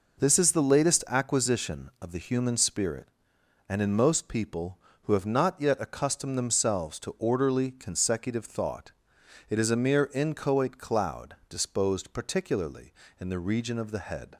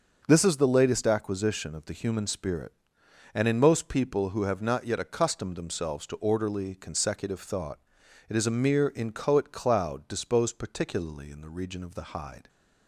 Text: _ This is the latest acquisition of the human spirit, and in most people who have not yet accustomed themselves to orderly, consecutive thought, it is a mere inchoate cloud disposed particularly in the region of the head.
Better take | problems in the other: first | says "hide" for "head"; at 12.1 s

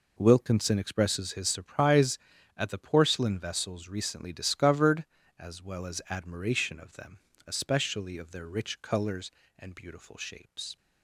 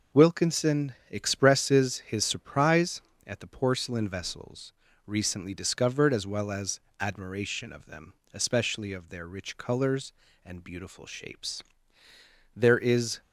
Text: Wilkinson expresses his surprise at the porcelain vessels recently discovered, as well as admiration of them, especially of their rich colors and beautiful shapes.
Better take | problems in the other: first | pauses between "Wilkinson" and "expresses"; slight; at 0.9 s; 0.16 s long // pauses between "vessels" and "recently"; slight; at 4.7 s; 0.32 s long // pauses between "as" and "admiration"; slight; at 6.7 s; 0.20 s long // goes on to say "There is"; noticeable; from 12.5 s on; 0.66 s long

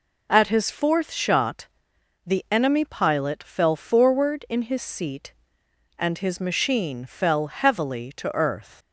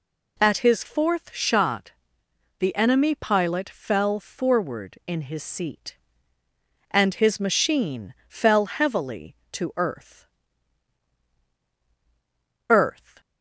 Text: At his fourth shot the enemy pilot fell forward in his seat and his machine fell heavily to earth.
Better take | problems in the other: first | pauses between "shot" and "the"; noticeable; at 1.9 s; 0.66 s long; noticeable in the first // pauses between "machine" and "fell"; slight; at 8.1 s; 0.16 s long // says "earth" twice; at 12.6 s

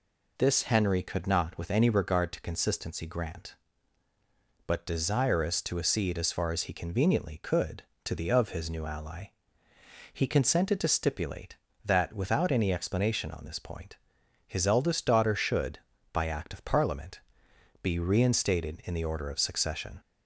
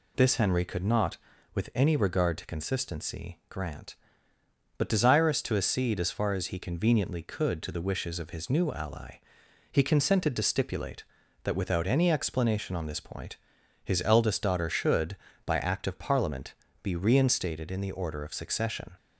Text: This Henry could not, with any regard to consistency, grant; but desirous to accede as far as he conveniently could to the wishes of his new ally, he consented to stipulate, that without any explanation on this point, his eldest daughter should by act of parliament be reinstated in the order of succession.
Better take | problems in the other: second | skips "wishes"; at 8.3 s // pauses between "parliament" and "be"; noticeable; at 17.1 s; 0.64 s long; slight in the second

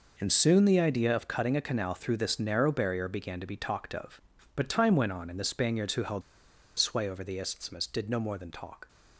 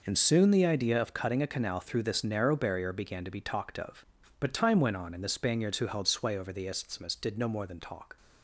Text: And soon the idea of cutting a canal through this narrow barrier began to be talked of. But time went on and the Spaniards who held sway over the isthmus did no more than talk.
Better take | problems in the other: second | pauses between "held" and "sway"; noticeable; at 6.2 s; 0.58 s long

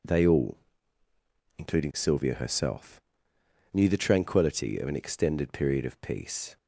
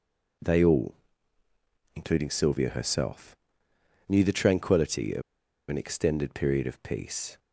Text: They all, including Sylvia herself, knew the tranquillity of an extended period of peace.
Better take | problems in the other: first | pauses between "of" and "an"; noticeable; at 5.2 s; 0.48 s long

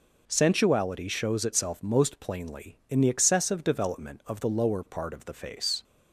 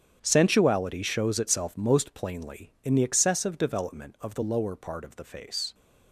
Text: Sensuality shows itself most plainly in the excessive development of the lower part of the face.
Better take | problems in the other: first | gets quieter; strong; throughout; 15 dB

